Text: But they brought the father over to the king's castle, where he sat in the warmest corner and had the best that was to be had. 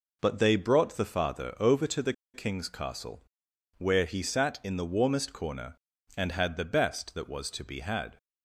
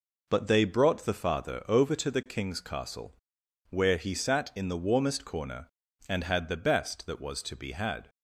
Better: second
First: pauses between "the" and "king's"; slight; at 2.1 s; 0.21 s long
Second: none

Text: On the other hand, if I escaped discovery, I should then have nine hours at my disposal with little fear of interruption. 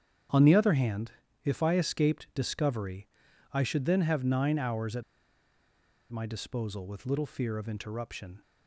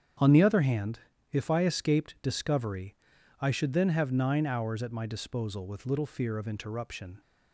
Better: second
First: starts louder than the rest; strong; until 1.6 s; 8.5 dB // pauses between "at" and "my"; at 5.0 s; 1.0 s long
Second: starts louder than the rest; strong; until 1.5 s; 8.5 dB

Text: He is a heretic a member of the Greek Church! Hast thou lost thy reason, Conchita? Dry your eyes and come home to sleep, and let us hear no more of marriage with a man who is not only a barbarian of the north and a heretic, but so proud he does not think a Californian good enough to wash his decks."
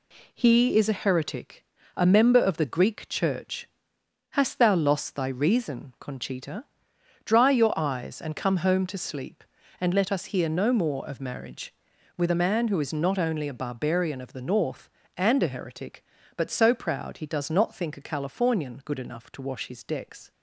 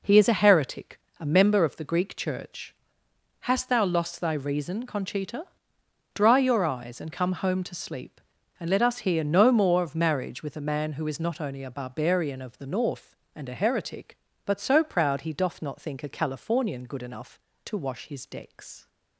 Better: first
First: pauses between "heretic" and "a"; slight; at 1.6 s; 0.30 s long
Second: pauses between "heretic" and "a"; slight; at 0.9 s; 0.22 s long // says "doth" for "does"; at 15.3 s

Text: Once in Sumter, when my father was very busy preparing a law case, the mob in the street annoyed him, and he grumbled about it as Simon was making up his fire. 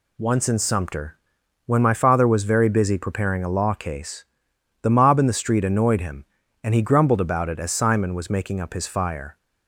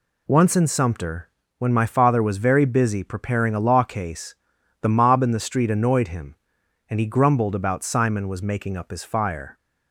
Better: first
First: none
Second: skips "it as"; at 7.8 s

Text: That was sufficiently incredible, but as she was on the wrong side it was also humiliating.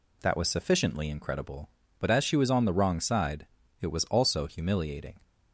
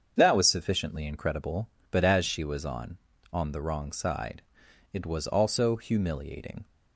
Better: first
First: pauses between "side" and "it"; slight; at 3.4 s; 0.34 s long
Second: starts louder than the rest; until 1.1 s; 7 dB // says "on" twice; at 3.3 s // pauses between "side" and "it"; noticeable; at 4.4 s; 0.50 s long

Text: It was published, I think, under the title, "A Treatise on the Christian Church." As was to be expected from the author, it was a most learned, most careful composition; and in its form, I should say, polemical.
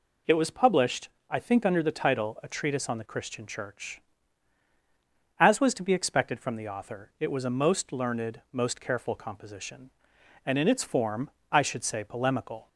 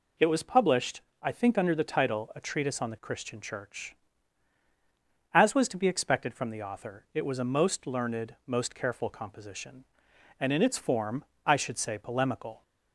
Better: neither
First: none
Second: none

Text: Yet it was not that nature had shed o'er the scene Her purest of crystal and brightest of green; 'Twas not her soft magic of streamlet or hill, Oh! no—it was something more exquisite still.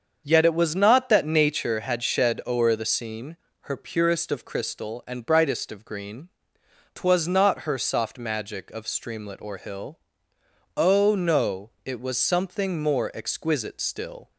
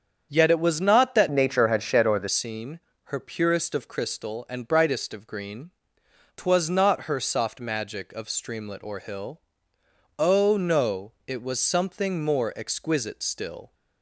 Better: first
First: starts louder than the rest; until 1.2 s; 7 dB // pauses between "scene" and "Her"; slight; at 3.3 s; 0.26 s long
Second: starts louder than the rest; strong; until 1.3 s; 7.5 dB // changes voice from "nature" to "the"; from 1.3 to 2.2 s; 0.9 s long // pauses between "scene" and "Her"; slight; at 2.7 s; 0.26 s long

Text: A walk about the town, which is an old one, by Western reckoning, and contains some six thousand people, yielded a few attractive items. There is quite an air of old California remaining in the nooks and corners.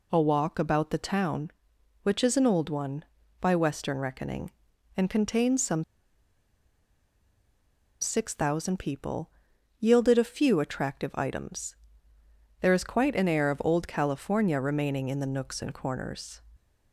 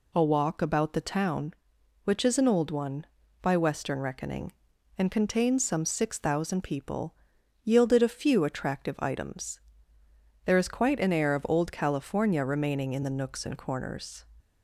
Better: second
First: pauses between "some" and "six"; strong; at 5.8 s; 2.1 s long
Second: none

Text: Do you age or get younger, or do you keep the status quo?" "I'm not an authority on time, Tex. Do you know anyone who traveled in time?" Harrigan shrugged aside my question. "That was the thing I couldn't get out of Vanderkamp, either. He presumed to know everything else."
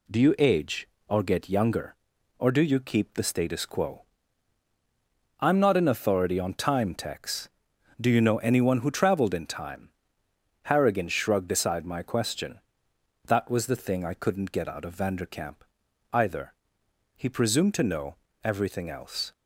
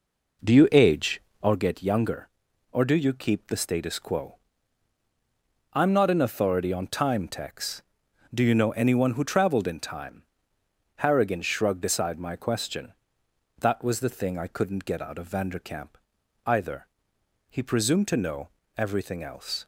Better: first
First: pauses between "know" and "everything"; slight; at 18.1 s; 0.30 s long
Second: starts louder than the rest; noticeable; until 1.6 s; 4.5 dB // pauses between "know" and "everything"; slight; at 18.4 s; 0.30 s long

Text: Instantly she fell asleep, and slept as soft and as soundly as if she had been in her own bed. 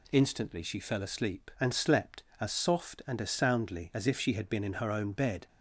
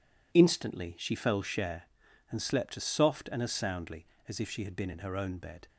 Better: first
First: none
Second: says "share" for "asleep"; at 1.4 s

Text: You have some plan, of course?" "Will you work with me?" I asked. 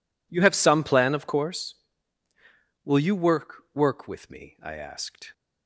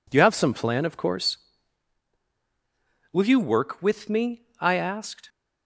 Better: second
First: says "work" twice; at 3.7 s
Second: none

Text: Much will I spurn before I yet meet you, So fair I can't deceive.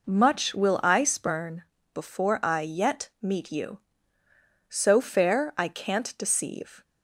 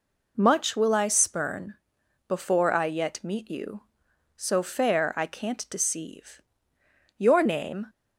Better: first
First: pauses between "spurn" and "before"; slight; at 1.6 s; 0.30 s long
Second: pauses between "spurn" and "before"; noticeable; at 1.7 s; 0.52 s long // goes on to say "Your name"; noticeable; from 7.1 s on; 0.66 s long

